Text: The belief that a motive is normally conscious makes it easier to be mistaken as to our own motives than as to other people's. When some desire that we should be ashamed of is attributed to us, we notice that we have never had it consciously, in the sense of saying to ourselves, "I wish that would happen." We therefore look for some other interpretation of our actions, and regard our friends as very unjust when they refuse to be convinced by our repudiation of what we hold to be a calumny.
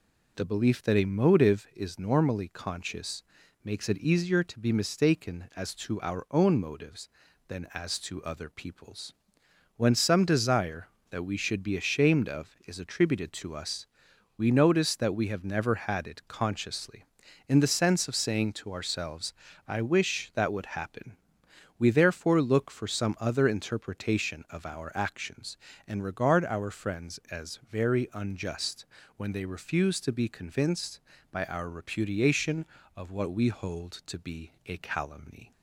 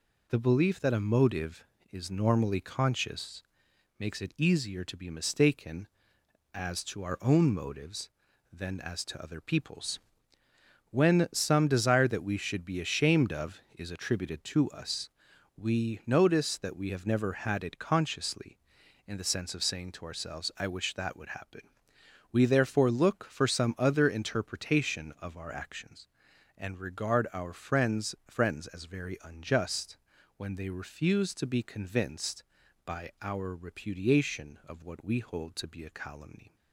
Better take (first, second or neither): first